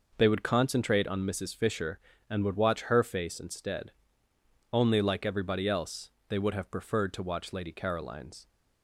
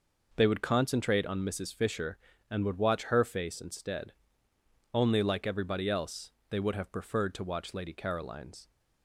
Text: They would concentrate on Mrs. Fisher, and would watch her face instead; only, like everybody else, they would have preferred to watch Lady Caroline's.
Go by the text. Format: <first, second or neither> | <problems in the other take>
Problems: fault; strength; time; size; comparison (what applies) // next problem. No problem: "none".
neither | none